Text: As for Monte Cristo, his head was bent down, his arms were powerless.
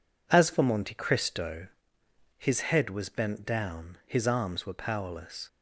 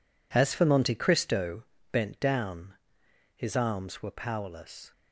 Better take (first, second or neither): first